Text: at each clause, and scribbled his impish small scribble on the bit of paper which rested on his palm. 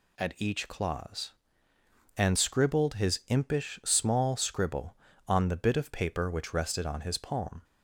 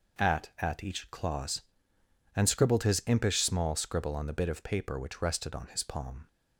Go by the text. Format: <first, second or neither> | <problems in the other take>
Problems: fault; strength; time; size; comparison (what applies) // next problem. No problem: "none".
first | says "at" twice; at 0.5 s